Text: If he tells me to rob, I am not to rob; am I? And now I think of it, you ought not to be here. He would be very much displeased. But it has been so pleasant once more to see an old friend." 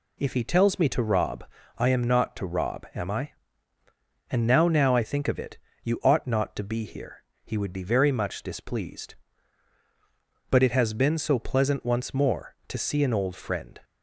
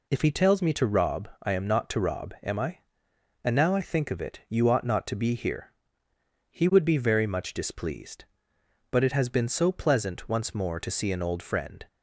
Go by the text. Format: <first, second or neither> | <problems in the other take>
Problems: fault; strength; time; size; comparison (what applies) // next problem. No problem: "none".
second | says "now" twice; at 4.6 s